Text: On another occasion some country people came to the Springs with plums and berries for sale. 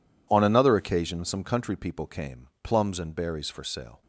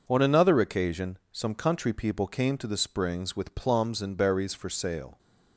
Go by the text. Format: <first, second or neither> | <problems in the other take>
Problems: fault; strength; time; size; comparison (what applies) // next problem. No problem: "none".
second | skips "to the Springs with"; at 2.5 s